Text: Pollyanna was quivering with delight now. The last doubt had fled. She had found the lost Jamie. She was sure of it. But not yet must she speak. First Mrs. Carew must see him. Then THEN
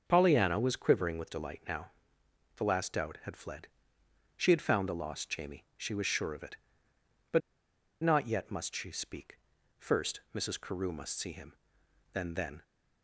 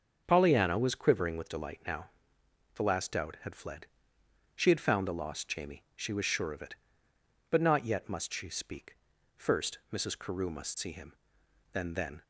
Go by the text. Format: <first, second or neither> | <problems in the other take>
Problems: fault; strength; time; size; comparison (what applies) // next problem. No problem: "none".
second | starts louder than the rest; until 1.0 s; 6.5 dB; also in the second // pauses between "But" and "not"; noticeable; at 7.4 s; 0.62 s long